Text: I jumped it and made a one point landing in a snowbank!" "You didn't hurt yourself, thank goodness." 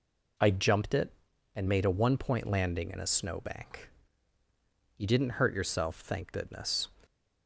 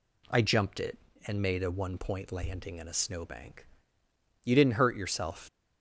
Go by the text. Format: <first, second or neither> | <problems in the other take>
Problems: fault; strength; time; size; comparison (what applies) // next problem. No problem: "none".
first | stops before "thank goodness"; at 5.4 s